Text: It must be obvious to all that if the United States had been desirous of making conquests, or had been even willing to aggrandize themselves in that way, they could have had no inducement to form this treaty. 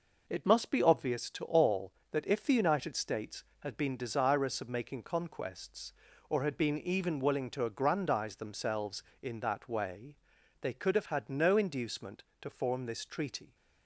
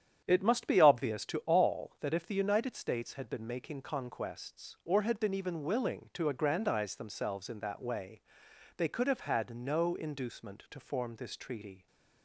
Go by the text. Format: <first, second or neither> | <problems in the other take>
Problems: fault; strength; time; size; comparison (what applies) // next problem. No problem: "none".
first | starts louder than the rest; strong; until 1.2 s; 9 dB // skips "desirous of"; at 3.4 s